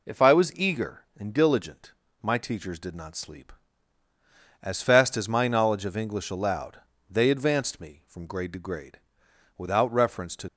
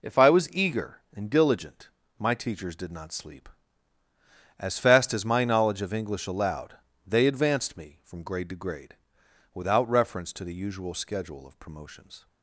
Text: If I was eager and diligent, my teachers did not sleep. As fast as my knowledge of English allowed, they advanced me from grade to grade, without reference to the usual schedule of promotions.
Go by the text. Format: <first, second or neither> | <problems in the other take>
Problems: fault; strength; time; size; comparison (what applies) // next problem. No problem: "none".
second | stops before "the usual schedule of promotions"; at 10.4 s